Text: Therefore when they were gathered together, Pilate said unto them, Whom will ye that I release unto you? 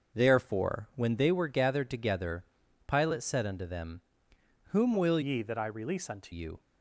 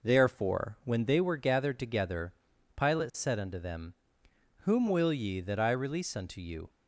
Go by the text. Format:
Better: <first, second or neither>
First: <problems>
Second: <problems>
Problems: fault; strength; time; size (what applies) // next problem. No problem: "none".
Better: second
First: starts louder than the rest; noticeable; until 1.2 s; 6 dB // changes voice from "ye" to "unto"; from 5.2 to 6.3 s; 1.1 s long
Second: none